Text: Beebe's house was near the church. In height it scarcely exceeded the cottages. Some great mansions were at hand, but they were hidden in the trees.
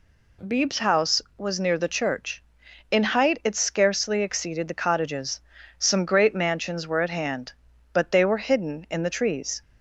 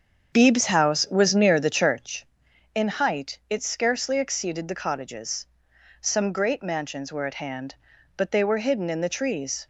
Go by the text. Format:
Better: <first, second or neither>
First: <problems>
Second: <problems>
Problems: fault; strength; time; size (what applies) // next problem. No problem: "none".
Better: first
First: none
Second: starts louder than the rest; strong; until 2.1 s; 7 dB